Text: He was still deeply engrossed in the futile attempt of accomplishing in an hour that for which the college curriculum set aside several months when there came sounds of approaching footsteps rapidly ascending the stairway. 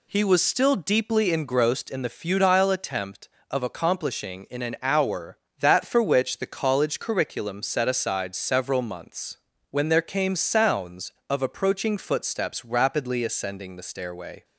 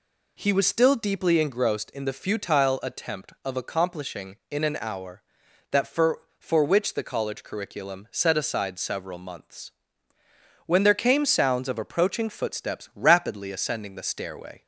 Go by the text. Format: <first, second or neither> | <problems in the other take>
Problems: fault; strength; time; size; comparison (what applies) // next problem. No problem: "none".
first | says "for" twice; at 6.3 s // pauses between "months" and "when"; noticeable; at 9.7 s; 0.96 s long; slight in the first